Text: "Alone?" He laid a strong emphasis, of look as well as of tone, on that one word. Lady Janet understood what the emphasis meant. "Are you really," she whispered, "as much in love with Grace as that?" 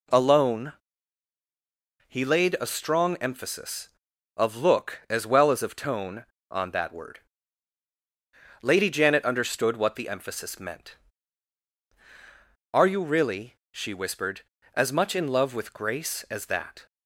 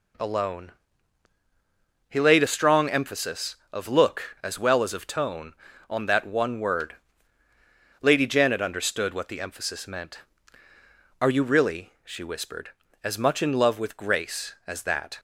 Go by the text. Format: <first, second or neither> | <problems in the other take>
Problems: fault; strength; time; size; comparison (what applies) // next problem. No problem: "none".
second | skips "one"; at 6.9 s